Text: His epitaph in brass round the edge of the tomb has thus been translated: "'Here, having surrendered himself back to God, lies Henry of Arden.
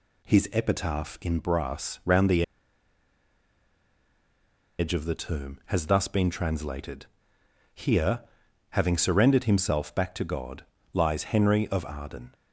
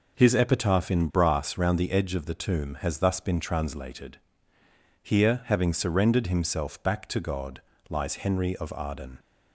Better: second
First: pauses between "the" and "edge"; strong; at 2.4 s; 2.3 s long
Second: none

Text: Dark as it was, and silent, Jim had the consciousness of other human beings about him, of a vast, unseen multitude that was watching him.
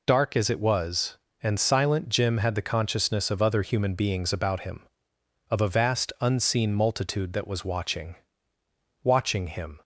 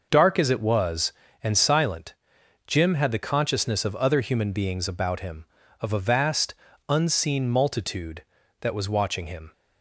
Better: second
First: says "watching" twice; at 9.0 s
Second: none

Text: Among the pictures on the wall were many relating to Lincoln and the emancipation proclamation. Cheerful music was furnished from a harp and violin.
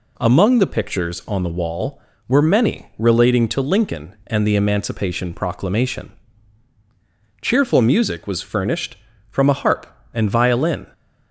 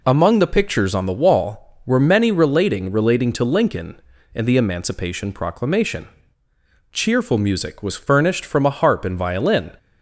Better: first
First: none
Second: says "relating" twice; at 2.8 s

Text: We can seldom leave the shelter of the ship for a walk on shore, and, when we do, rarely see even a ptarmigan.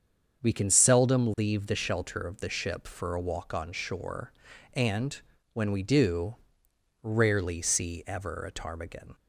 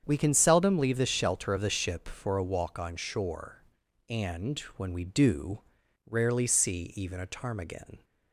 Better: second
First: starts louder than the rest; until 1.4 s; 7 dB // says "ever" for "even"; at 8.0 s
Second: starts louder than the rest; strong; until 1.0 s; 8 dB

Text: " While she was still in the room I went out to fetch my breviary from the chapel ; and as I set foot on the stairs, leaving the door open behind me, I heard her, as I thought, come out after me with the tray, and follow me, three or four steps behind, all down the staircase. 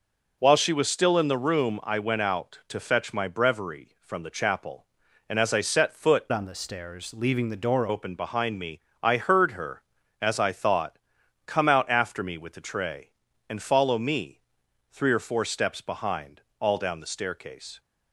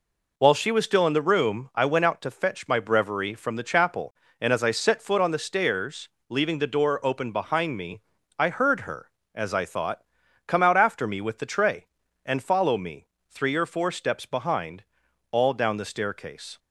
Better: second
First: changes voice from "on" to "door"; from 6.2 to 7.8 s; 1.6 s long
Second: none

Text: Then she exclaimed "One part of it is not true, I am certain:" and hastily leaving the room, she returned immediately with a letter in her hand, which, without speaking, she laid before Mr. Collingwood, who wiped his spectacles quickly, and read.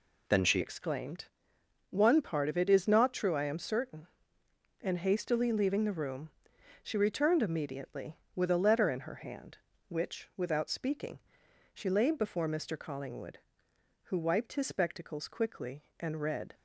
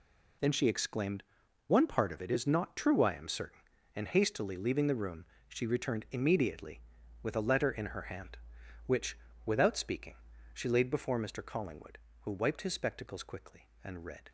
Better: second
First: changes voice at "exclaimed"; from 0.6 s on; 15.9 s long // pauses between "exclaimed" and "One"; noticeable; at 1.2 s; 0.64 s long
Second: pauses between "exclaimed" and "One"; at 1.2 s; 0.44 s long

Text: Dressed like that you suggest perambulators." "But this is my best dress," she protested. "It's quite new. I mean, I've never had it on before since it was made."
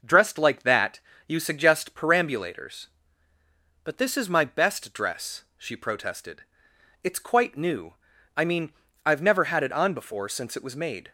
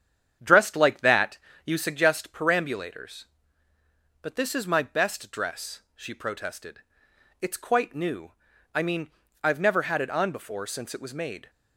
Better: first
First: pauses between "that" and "you"; slight; at 0.9 s; 0.26 s long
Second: starts louder than the rest; strong; until 2.0 s; 8.5 dB // pauses between "that" and "you"; slight; at 1.3 s; 0.26 s long

